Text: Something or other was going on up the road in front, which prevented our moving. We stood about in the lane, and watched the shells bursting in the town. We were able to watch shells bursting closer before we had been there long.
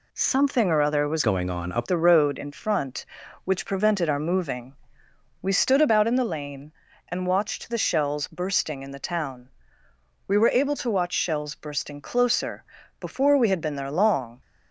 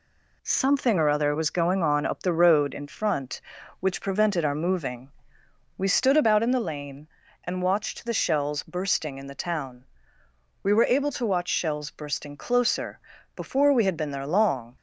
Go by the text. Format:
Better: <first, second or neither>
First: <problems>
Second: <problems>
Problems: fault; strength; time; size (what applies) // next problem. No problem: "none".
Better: second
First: changes voice from "going" to "up"; from 1.2 to 1.8 s; 0.6 s long // pauses between "closer" and "before"; slight; at 12.6 s; 0.34 s long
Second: pauses between "closer" and "before"; slight; at 13.0 s; 0.34 s long